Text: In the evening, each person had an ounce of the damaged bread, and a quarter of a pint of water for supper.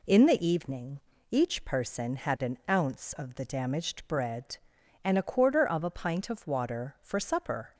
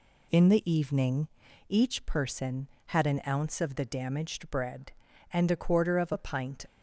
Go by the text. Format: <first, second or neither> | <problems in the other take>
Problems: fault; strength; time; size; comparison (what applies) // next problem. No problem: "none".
first | stops before "of water for supper"; at 6.6 s